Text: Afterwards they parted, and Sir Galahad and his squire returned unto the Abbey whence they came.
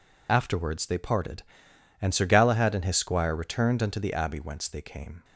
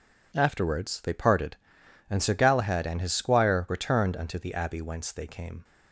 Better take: second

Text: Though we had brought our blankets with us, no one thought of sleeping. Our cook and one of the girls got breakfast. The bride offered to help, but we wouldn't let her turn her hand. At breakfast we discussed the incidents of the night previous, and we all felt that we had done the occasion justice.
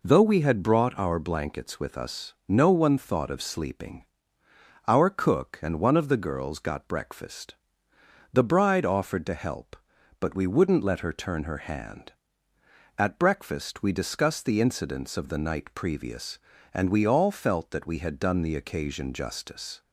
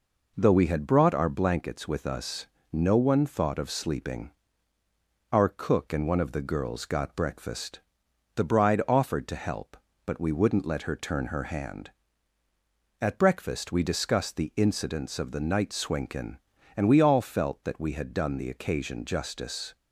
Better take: first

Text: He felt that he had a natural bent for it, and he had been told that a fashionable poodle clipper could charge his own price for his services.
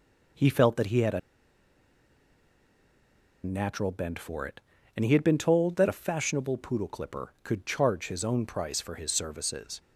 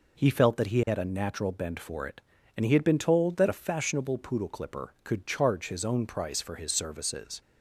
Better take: second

